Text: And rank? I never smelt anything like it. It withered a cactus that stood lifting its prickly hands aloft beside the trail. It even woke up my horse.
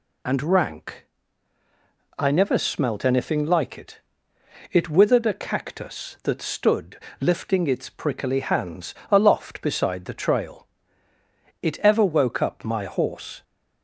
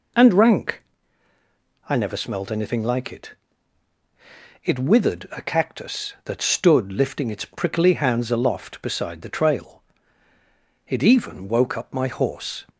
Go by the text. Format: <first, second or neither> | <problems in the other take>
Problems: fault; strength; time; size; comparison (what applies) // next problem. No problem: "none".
second | pauses between "stood" and "lifting"; slight; at 6.9 s; 0.22 s long // pauses between "hands" and "aloft"; slight; at 8.9 s; 0.18 s long // says "ever" for "even"; at 11.7 s